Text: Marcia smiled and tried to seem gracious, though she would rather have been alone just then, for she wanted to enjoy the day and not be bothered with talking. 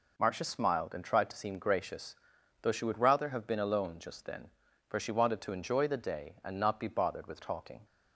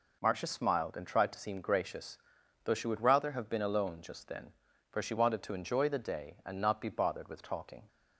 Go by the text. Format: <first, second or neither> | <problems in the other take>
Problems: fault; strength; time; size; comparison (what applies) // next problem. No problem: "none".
neither | none